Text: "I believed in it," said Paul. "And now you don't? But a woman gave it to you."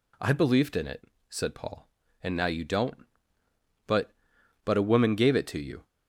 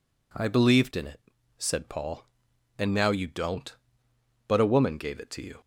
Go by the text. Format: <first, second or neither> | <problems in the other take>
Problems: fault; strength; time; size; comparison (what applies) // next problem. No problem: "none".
second | says "But" twice; at 4.6 s